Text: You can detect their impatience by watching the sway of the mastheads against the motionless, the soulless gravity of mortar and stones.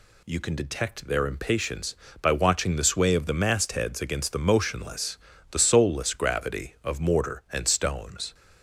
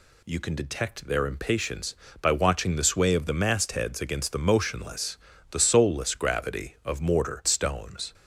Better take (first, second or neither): first